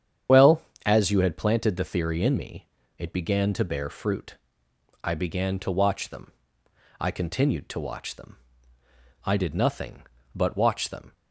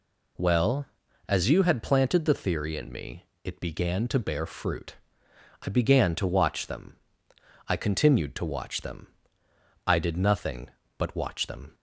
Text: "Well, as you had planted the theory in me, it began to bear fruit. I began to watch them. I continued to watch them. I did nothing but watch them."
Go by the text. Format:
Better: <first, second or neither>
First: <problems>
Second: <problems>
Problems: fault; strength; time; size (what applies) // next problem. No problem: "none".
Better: second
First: loses the start of "Well"; at 0.2 s; 35 ms // starts louder than the rest; strong; until 1.5 s; 8.5 dB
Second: none